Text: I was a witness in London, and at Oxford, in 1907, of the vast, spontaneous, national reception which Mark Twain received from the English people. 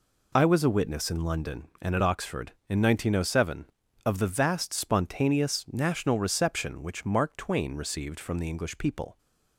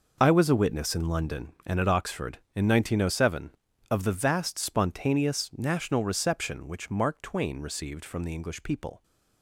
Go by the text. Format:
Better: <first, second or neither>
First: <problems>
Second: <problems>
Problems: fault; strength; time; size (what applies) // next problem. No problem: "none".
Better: first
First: none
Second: gets quieter; strong; throughout; 12.5 dB